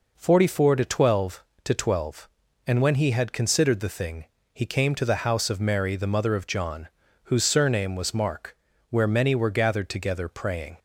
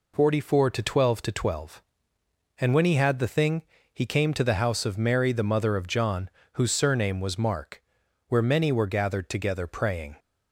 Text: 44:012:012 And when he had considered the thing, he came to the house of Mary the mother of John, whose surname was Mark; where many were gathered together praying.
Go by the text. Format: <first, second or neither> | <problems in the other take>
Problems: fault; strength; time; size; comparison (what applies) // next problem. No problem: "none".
first | skips "considered"; at 3.1 s